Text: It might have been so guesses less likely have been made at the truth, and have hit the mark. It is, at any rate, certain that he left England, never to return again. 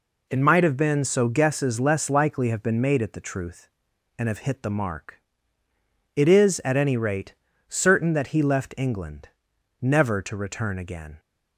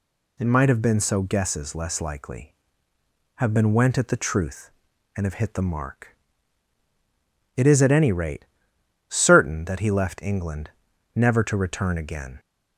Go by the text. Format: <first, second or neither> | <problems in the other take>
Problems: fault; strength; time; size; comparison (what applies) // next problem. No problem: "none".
first | says "went" for "made"; at 3.7 s